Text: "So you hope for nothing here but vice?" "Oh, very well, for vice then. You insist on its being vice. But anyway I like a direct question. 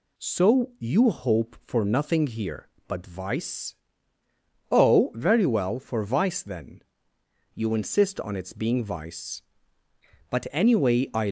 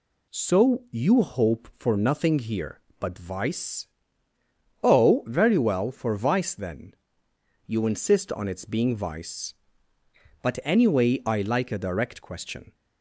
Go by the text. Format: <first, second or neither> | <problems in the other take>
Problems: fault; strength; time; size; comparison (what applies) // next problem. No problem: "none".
second | stops before "like a direct question"; at 11.2 s